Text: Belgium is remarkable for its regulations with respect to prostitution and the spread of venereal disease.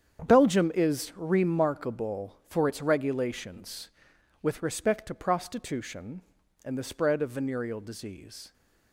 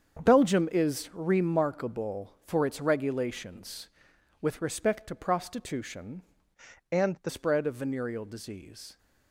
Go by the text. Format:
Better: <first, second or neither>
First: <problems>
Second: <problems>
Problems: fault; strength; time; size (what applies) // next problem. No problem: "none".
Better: first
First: starts louder than the rest; strong; until 1.3 s; 8 dB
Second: starts louder than the rest; strong; until 1.3 s; 7.5 dB // changes voice from "and" to "the"; from 6.9 to 7.3 s; 0.4 s long